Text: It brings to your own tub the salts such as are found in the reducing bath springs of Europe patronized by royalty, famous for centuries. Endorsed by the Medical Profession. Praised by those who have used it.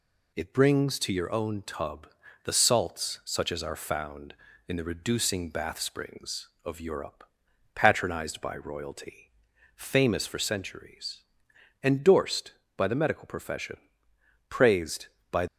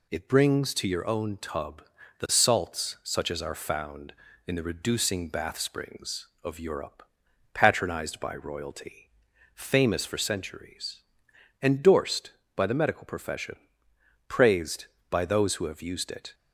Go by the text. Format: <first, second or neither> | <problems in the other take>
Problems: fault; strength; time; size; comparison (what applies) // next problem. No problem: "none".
second | pauses between "tub" and "the"; at 2.0 s; 0.38 s long; also in the second // pauses between "Europe" and "patronized"; noticeable; at 7.2 s; 0.50 s long; noticeable in the second // stops before "those who have used it"; at 15.4 s